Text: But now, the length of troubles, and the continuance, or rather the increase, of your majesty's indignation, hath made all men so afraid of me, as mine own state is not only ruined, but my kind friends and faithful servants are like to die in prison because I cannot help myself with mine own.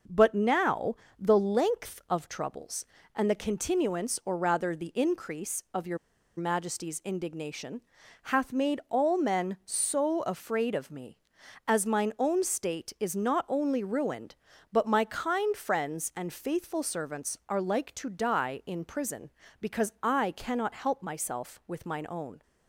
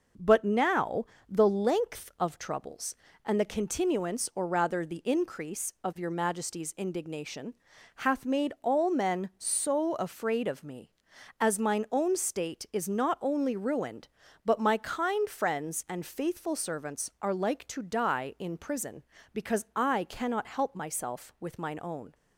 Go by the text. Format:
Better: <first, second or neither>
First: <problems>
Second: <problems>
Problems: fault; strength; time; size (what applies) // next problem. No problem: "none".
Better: second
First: pauses between "your" and "majesty's"; at 5.9 s; 0.39 s long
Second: none